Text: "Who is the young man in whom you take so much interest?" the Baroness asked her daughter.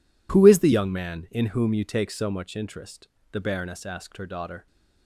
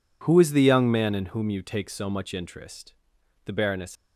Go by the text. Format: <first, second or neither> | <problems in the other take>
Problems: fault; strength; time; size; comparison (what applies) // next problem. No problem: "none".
first | stops before "asked her daughter"; at 3.9 s